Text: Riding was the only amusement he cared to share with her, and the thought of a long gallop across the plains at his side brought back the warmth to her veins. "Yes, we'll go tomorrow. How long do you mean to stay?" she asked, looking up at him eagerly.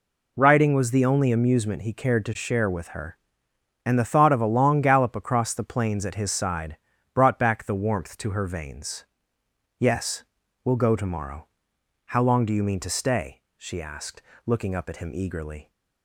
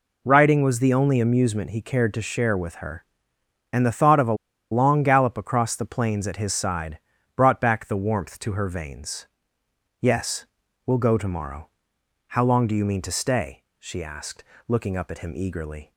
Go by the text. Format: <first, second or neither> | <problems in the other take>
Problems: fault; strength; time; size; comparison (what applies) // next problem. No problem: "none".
first | pauses between "a" and "long"; at 4.3 s; 0.36 s long // pauses between "side" and "brought"; at 6.9 s; 0.38 s long; also in the first